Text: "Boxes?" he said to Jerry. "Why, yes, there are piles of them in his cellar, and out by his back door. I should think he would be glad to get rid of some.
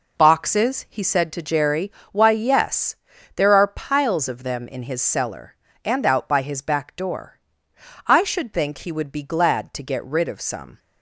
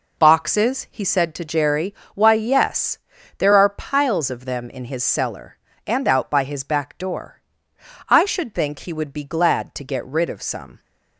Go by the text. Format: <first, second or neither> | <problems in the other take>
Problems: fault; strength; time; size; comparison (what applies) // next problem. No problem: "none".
neither | none